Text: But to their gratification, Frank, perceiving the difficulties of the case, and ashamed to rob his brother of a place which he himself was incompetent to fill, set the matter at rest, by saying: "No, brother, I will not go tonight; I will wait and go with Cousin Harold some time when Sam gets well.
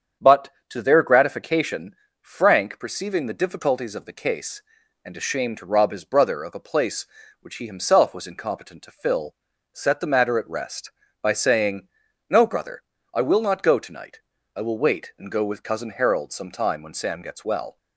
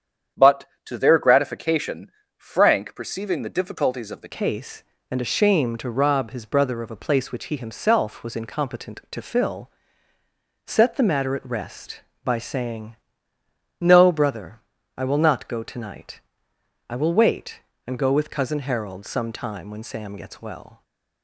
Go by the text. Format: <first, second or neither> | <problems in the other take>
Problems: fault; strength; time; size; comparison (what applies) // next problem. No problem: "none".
first | starts louder than the rest; strong; until 1.5 s; 8.5 dB; strong in the first // changes voice at "case"; from 4.3 s on; 16.5 s long